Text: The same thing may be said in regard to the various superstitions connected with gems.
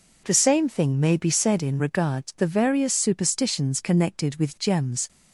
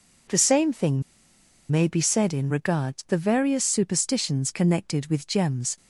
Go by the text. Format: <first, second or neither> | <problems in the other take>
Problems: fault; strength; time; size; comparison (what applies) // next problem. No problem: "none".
first | pauses between "thing" and "may"; noticeable; at 1.0 s; 0.69 s long